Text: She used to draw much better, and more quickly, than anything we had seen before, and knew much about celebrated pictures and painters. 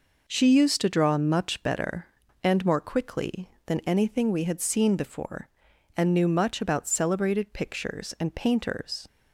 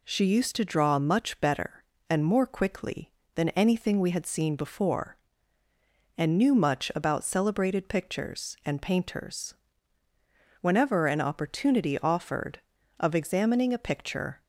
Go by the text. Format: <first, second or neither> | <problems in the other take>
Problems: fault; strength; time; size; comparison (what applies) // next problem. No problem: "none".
first | goes on to say "Whenever an opportunity offered of examining a picture"; strong; from 10.6 s on; 3.8 s long